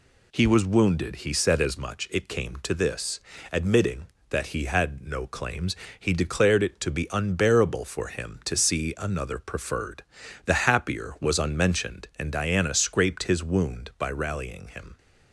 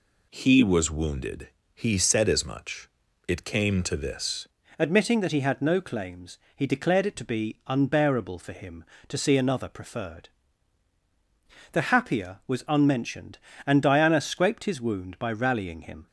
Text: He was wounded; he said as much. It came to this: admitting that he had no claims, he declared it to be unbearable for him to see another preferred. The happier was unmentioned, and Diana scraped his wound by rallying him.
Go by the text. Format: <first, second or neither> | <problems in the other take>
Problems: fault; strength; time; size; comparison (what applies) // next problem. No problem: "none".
first | changes voice at "admitting"; from 4.7 s on; 11.3 s long